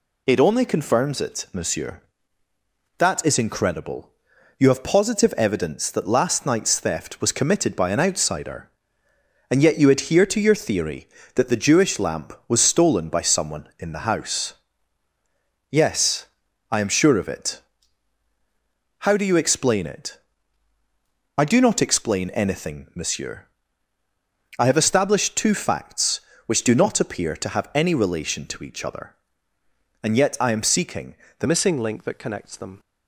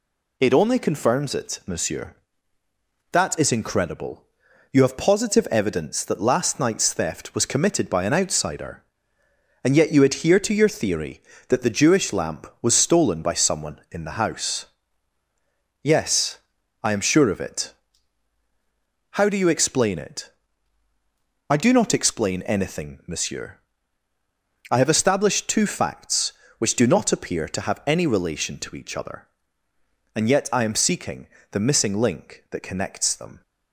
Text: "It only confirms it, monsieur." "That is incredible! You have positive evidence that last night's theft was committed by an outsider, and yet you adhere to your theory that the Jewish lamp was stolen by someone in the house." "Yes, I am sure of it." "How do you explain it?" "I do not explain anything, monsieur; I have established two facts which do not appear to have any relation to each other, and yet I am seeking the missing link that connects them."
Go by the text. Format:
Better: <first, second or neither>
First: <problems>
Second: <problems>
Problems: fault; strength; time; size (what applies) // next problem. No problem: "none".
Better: second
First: pauses between "seeking" and "the"; slight; at 31.1 s; 0.22 s long // changes voice at "missing"; from 31.4 s on; 1.3 s long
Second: pauses between "seeking" and "the"; slight; at 31.2 s; 0.22 s long